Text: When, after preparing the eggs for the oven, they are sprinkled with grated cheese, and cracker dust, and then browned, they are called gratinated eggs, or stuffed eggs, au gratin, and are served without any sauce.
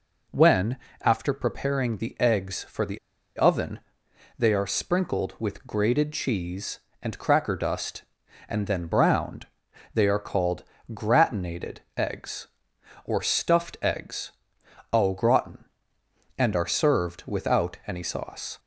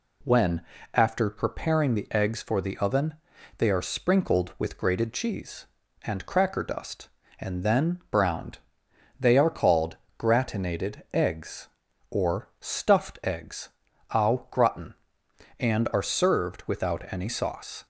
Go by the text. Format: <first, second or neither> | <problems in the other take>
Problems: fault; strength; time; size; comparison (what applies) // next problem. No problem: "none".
second | pauses between "the" and "oven"; at 2.9 s; 0.38 s long // pauses between "called" and "gratinated"; slight; at 10.6 s; 0.28 s long; slight in the second // pauses between "gratinated" and "eggs"; slight; at 11.7 s; 0.18 s long